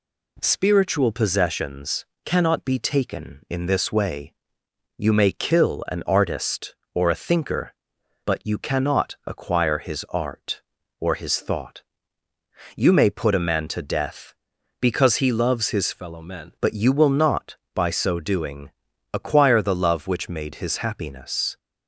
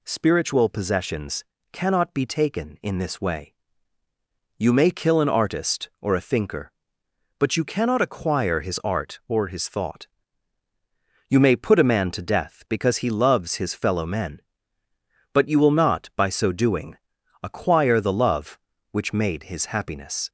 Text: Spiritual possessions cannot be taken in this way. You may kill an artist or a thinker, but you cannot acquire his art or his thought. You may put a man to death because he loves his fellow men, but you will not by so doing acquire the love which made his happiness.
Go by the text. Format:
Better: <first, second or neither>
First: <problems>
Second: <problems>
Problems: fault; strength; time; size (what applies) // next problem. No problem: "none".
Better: second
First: pauses between "possessions" and "cannot"; slight; at 2.0 s; 0.18 s long // changes voice from "fellow" to "men"; from 15.9 to 16.5 s; 0.6 s long // pauses between "doing" and "acquire"; at 18.7 s; 0.42 s long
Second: pauses between "possessions" and "cannot"; slight; at 1.4 s; 0.28 s long // pauses between "doing" and "acquire"; noticeable; at 16.9 s; 0.46 s long